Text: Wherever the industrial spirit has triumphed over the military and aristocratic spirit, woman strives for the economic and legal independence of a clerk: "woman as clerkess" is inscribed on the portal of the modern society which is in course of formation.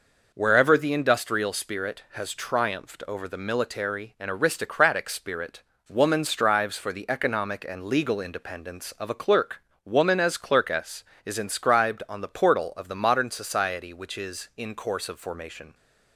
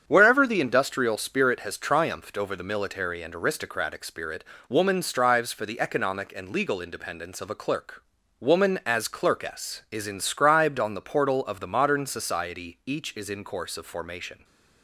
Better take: first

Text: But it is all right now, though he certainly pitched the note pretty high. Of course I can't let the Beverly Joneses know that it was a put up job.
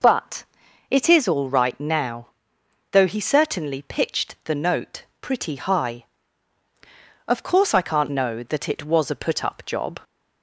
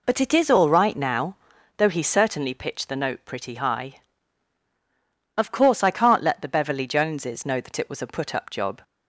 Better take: second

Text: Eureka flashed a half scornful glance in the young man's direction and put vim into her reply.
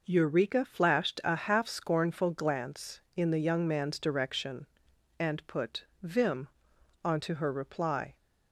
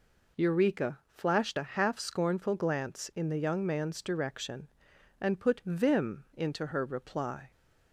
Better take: second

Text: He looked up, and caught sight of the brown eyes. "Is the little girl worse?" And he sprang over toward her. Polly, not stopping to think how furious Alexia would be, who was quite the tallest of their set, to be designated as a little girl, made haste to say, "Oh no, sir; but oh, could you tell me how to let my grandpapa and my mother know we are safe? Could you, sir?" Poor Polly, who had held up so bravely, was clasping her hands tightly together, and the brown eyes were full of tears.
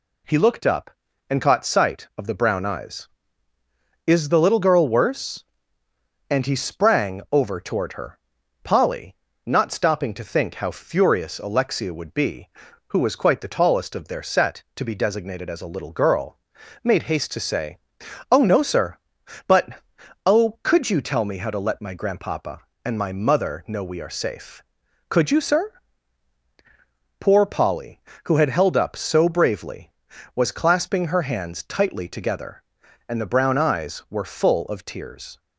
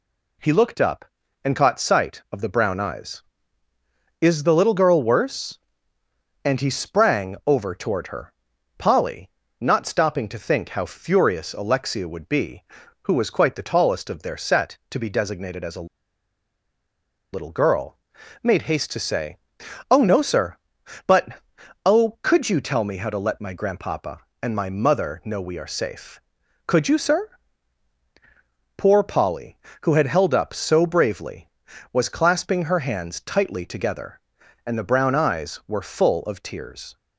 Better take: first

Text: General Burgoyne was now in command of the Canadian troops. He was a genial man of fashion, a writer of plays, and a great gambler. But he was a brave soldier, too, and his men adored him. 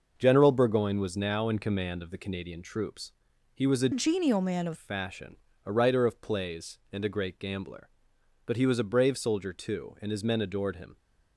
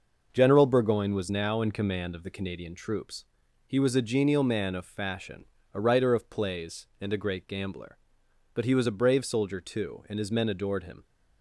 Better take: second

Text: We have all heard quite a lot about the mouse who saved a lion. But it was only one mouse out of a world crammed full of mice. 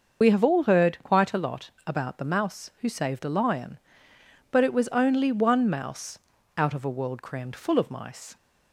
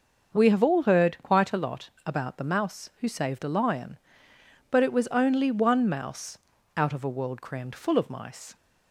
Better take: second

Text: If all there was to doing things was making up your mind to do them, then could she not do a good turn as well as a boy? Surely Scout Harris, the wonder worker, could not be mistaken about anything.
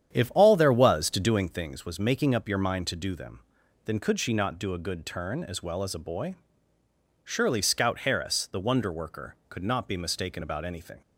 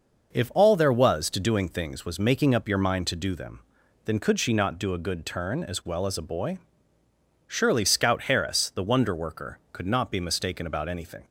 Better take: second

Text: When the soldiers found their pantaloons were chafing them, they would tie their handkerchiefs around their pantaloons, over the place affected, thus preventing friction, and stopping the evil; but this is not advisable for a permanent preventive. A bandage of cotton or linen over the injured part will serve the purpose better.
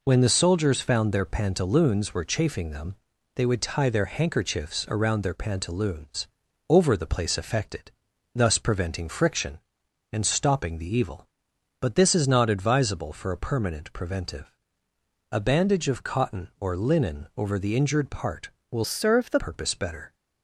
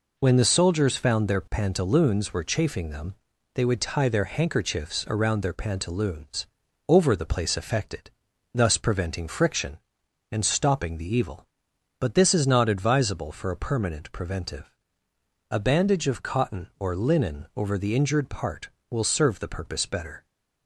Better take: second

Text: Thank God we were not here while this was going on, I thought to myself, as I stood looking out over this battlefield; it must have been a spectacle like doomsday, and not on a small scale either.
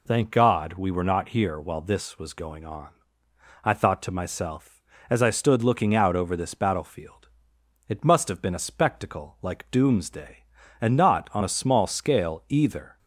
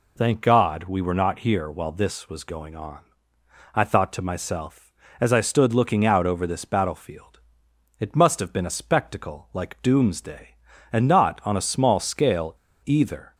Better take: first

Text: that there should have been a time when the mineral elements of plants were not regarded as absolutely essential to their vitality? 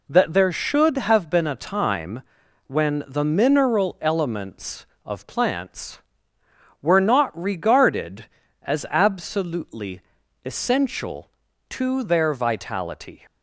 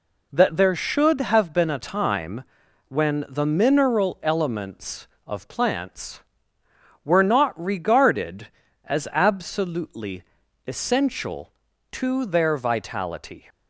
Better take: neither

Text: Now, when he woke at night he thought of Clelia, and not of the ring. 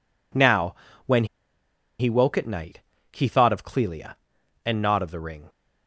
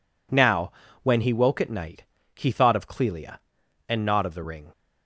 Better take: second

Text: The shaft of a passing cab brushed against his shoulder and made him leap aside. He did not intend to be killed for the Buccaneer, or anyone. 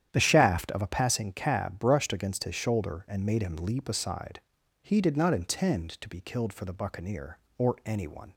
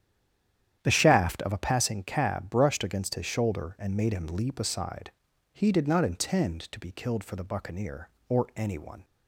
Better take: first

